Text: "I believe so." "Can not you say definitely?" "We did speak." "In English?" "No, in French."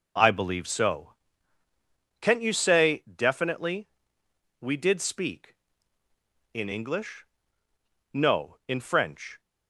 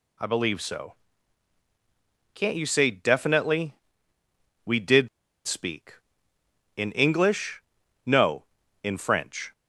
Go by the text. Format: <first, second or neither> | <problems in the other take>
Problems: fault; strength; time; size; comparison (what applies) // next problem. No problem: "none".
first | pauses between "did" and "speak"; at 5.0 s; 0.39 s long